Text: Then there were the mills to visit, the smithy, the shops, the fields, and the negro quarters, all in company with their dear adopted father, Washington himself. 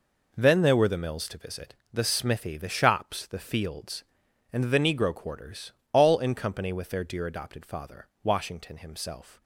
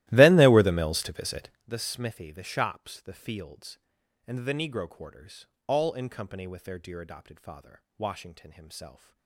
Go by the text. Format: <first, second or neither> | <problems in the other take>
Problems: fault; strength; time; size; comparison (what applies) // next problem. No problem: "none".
first | starts louder than the rest; strong; until 1.7 s; 16 dB